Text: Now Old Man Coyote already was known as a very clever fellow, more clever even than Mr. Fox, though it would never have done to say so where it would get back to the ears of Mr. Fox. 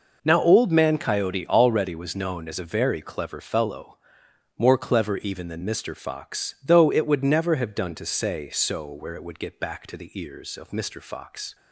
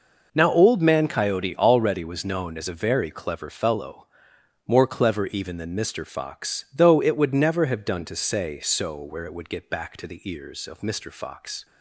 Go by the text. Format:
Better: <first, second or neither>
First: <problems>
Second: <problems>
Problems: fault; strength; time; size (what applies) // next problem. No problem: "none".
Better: neither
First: none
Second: none